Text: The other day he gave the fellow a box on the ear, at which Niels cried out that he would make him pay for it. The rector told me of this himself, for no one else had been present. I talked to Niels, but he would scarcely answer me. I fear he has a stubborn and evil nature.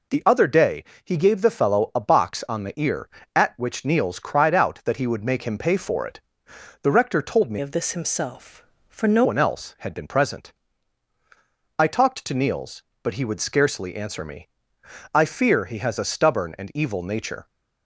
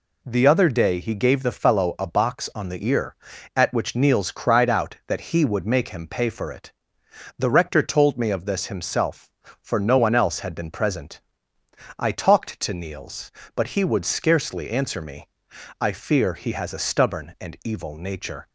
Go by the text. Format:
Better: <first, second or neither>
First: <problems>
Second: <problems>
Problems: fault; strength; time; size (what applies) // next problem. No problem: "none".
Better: second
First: pauses between "day" and "he"; slight; at 0.8 s; 0.20 s long // changes voice from "of" to "no"; from 7.6 to 9.2 s; 1.6 s long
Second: none